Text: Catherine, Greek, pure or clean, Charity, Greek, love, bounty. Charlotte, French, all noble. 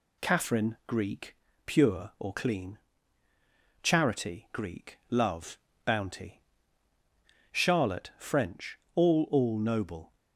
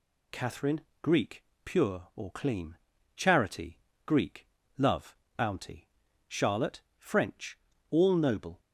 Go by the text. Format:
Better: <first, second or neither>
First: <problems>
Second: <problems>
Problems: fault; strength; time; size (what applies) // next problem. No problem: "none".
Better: second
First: says "all" twice; at 9.2 s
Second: none